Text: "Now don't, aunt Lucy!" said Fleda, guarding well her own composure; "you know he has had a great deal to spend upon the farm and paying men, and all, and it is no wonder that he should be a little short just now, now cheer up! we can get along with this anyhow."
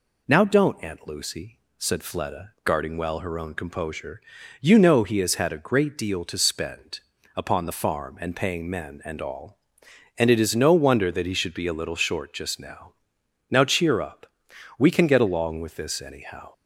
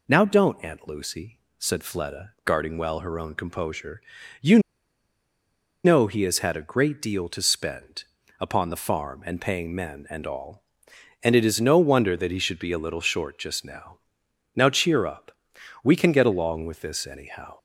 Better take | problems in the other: first | pauses between "you" and "know"; strong; at 4.5 s; 1.2 s long // pauses between "spend" and "upon"; slight; at 8.0 s; 0.36 s long; slight in the first

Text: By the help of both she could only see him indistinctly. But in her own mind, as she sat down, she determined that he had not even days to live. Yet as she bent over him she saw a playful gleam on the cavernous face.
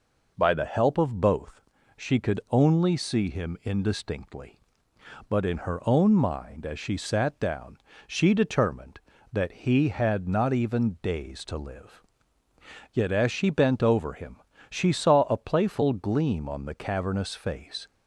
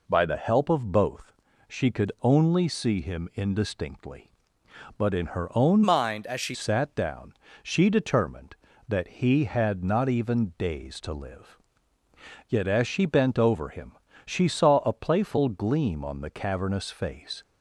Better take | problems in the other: first | pauses between "both" and "she"; slight; at 1.3 s; 0.36 s long; slight in the first // changes voice from "mind" to "she"; from 5.8 to 6.5 s; 0.7 s long // pauses between "him" and "she"; slight; at 13.9 s; 0.32 s long; slight in the first

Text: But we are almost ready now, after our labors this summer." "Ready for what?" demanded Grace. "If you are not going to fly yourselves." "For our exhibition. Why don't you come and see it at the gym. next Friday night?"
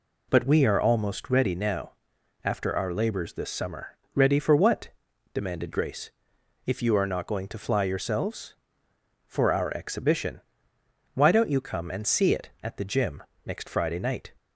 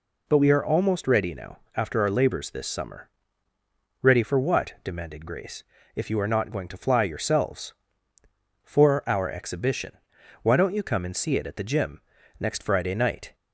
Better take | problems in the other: neither | none

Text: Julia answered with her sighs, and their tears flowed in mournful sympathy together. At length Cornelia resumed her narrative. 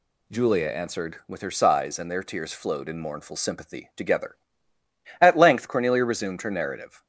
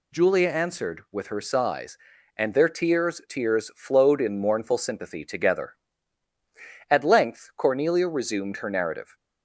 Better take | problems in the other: first | says "tears" twice; at 3.2 s

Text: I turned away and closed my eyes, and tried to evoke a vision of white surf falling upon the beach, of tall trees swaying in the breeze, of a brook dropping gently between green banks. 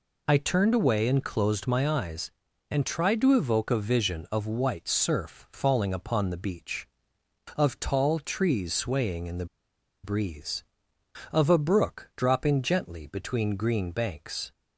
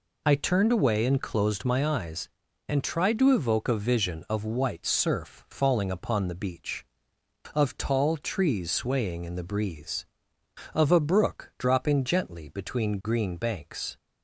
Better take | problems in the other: second | pauses between "the" and "breeze"; noticeable; at 9.4 s; 0.58 s long

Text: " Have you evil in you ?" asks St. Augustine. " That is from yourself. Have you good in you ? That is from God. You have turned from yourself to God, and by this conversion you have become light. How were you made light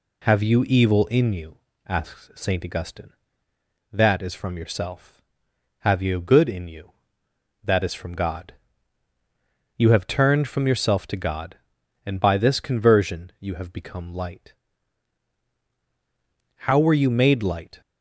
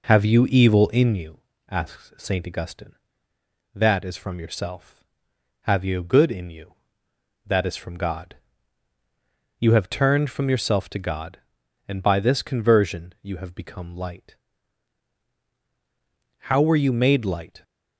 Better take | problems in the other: first | starts louder than the rest; noticeable; until 1.3 s; 4.5 dB

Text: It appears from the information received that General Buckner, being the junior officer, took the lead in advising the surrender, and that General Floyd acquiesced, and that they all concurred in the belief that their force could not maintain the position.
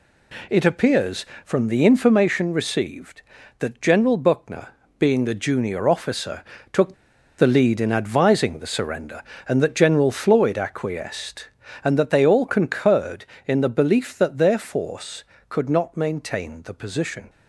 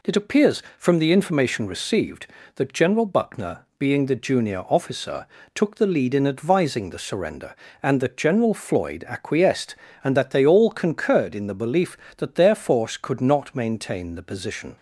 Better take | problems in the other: second | pauses between "took" and "the"; at 6.9 s; 0.44 s long

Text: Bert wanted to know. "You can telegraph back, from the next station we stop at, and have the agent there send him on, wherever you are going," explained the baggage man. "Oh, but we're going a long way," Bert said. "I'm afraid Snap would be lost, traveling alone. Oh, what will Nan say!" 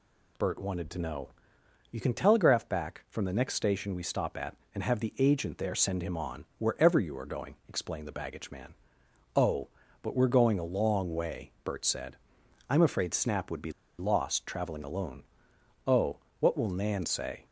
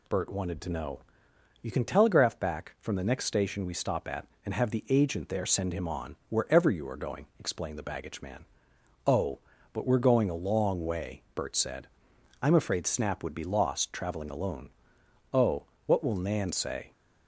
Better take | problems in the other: second | pauses between "be" and "lost"; slight; at 13.7 s; 0.27 s long

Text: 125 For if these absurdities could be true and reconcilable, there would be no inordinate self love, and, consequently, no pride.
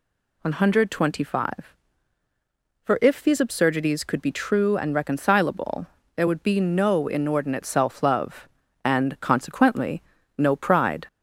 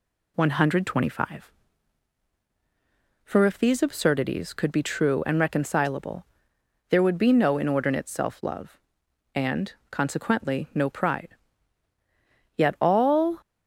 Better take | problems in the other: first | goes on to say "Yet all"; noticeable; from 12.5 s on; 0.86 s long

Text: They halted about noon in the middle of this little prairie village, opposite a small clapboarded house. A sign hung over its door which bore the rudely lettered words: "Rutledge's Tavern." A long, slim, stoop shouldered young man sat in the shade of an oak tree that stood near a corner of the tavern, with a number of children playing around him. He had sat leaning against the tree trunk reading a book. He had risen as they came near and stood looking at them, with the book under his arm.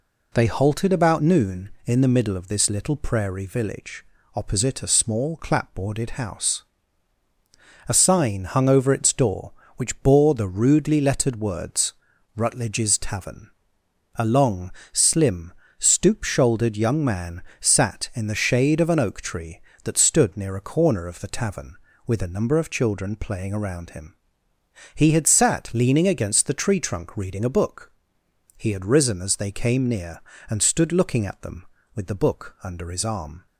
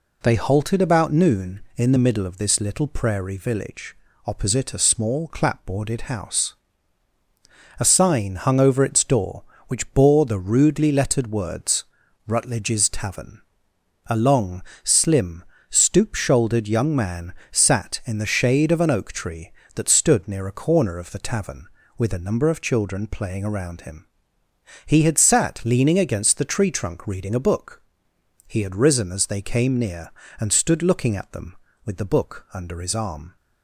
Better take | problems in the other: neither | pauses between "man" and "sat"; slight; the same in both

